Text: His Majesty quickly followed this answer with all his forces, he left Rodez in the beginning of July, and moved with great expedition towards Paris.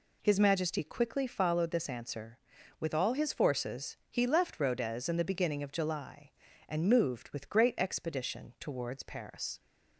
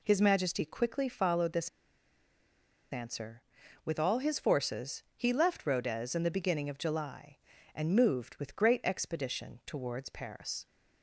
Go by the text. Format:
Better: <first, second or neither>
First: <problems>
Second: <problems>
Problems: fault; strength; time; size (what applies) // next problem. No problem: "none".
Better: first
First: none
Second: pauses between "this" and "answer"; at 1.6 s; 1.2 s long